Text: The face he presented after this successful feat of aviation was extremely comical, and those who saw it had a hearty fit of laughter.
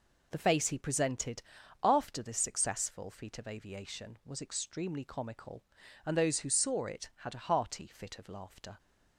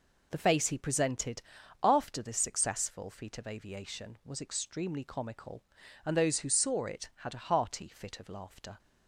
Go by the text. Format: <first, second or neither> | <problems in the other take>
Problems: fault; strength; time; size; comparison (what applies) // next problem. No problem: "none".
neither | pauses between "presented" and "after"; the same in both